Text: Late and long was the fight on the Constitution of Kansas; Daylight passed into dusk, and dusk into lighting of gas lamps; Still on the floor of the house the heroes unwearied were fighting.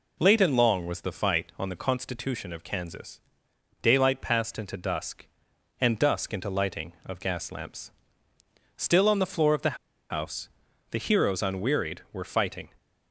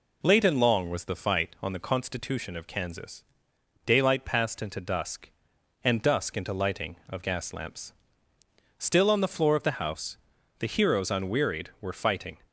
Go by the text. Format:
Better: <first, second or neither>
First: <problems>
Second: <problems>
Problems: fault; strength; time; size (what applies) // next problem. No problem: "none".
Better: second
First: pauses between "the" and "house"; slight; at 9.7 s; 0.35 s long // pauses between "house" and "the"; at 10.4 s; 0.44 s long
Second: pauses between "house" and "the"; at 10.1 s; 0.44 s long